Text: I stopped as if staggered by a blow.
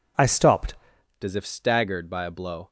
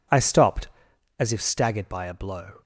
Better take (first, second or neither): second